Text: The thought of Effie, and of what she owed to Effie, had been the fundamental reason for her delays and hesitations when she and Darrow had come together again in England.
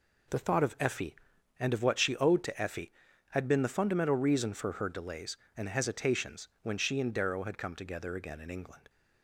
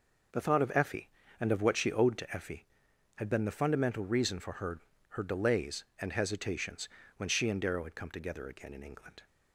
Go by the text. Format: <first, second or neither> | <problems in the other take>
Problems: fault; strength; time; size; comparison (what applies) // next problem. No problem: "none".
first | says "her" twice; at 5.0 s // pauses between "hesitations" and "when"; slight; at 6.8 s; 0.30 s long